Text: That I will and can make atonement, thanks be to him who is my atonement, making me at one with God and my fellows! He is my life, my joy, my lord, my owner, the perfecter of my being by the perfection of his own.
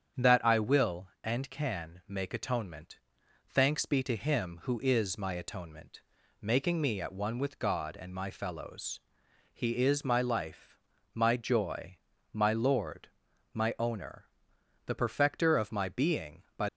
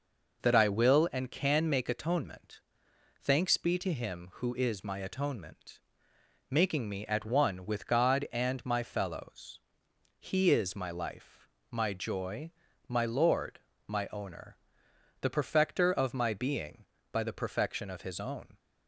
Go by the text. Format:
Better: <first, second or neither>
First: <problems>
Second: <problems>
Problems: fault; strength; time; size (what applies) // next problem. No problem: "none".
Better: second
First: starts louder than the rest; strong; until 1.3 s; 8 dB // stops before "the perfection of his own"; at 16.6 s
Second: none